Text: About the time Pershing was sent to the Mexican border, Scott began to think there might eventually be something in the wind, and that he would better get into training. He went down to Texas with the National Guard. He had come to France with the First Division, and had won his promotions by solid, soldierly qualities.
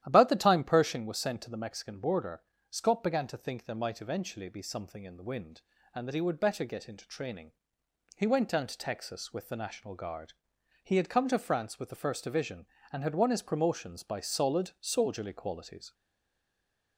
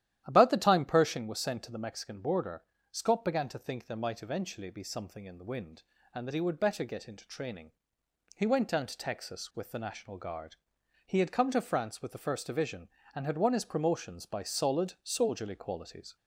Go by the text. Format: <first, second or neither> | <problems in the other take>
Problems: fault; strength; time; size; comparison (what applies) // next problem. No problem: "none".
second | starts louder than the rest; strong; until 1.0 s; 12 dB; strong in the second // stays silent after the last word; from 15.9 s on; 1.0 s long